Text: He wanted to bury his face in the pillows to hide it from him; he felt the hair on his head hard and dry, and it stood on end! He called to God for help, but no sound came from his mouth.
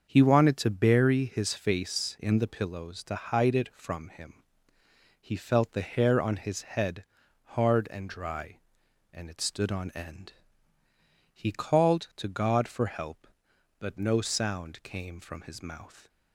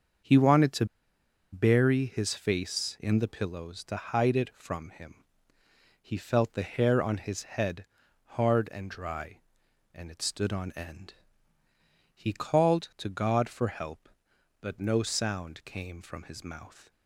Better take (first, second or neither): first